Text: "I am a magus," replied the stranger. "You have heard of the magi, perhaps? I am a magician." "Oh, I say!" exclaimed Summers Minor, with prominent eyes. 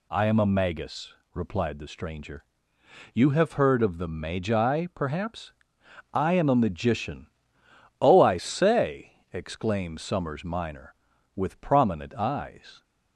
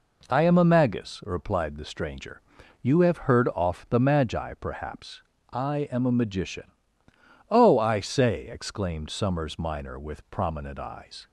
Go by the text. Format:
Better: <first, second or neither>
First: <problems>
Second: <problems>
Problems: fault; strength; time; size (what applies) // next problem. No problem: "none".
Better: first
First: none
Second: says "off" for "of"; at 3.5 s